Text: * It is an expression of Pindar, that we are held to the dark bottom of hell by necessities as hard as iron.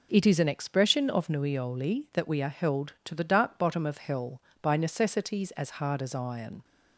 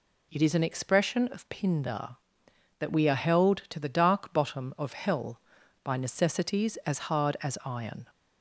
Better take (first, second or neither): second